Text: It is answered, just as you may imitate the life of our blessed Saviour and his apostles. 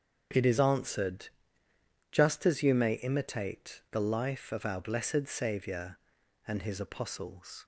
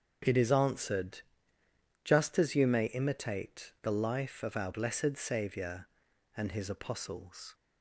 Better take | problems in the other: neither | starts louder than the rest; strong; the same in both

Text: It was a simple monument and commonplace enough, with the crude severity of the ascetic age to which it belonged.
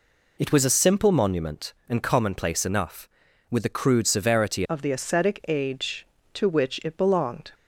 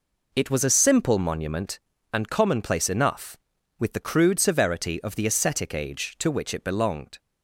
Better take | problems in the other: second | changes voice at "of"; from 4.6 s on; 2.9 s long

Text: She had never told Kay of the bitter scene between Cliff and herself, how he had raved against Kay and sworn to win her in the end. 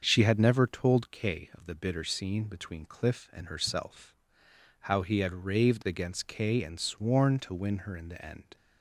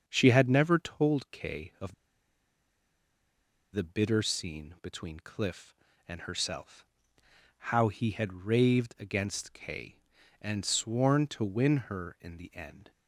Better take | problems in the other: first | starts louder than the rest; until 1.0 s; 6.5 dB; also in the first // pauses between "of" and "the"; strong; at 1.9 s; 1.7 s long

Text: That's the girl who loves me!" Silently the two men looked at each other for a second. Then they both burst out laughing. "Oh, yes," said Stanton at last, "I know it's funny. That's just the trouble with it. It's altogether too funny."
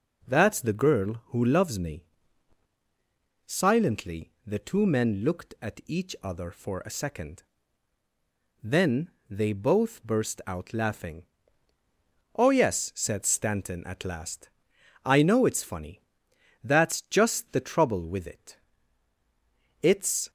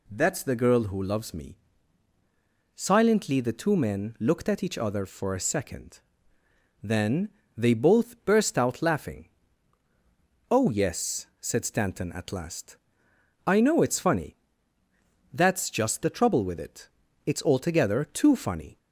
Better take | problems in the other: second | pauses between "Then" and "they"; slight; at 9.1 s; 0.20 s long; slight in the second // stops before "altogether too funny"; at 20.2 s

